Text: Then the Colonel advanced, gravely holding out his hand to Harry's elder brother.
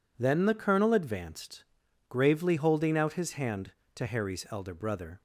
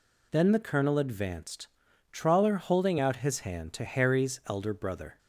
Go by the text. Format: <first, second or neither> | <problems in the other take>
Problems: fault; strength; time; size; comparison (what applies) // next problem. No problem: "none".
first | says "trawler" for "gravely"; at 2.1 s